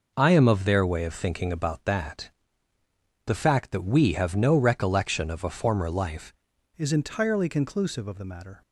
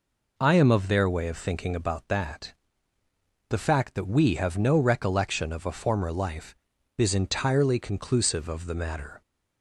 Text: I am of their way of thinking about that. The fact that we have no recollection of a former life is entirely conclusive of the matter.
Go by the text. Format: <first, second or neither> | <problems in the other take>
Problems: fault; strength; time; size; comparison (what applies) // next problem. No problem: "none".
second | changes voice at "is"; from 6.7 s on; 1.9 s long